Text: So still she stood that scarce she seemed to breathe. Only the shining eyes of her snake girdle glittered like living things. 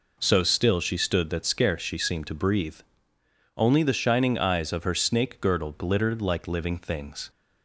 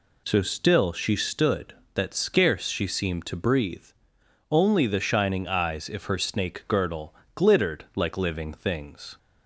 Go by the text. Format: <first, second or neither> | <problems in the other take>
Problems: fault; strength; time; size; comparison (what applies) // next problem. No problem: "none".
first | says "if" for "of"; at 5.8 s // pauses between "girdle" and "glittered"; slight; at 7.1 s; 0.22 s long